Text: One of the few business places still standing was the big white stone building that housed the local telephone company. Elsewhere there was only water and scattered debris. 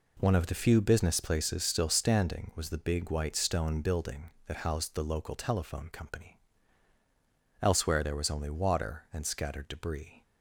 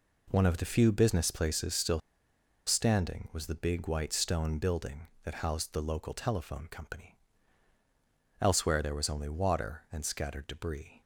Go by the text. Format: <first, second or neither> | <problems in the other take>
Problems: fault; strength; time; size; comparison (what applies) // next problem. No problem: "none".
first | pauses between "still" and "standing"; noticeable; at 2.0 s; 0.66 s long